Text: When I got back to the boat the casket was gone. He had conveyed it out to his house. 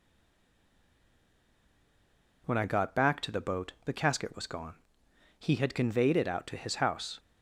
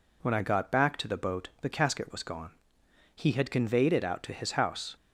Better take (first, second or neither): second